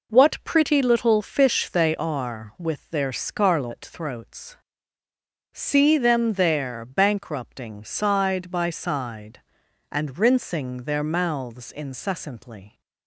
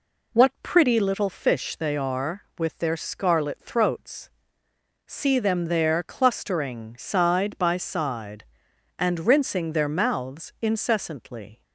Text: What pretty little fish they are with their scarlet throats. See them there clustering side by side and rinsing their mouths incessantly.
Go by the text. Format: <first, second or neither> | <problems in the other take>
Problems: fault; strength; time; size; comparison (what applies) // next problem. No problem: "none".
second | says "bankrupting" for "clustering"; at 6.8 s